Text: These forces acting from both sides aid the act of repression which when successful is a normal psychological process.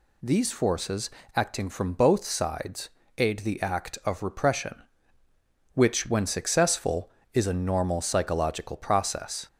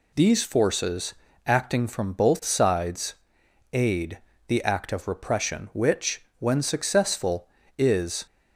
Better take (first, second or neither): first